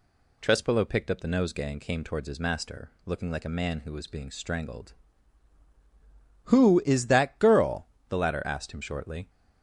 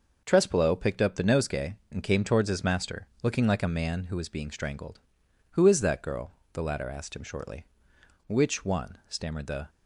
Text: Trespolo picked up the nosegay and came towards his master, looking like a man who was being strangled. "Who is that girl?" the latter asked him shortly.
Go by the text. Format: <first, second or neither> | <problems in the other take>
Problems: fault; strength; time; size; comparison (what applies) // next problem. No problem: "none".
first | goes on to say "Which one stammered the"; from 8.2 s on; 1.4 s long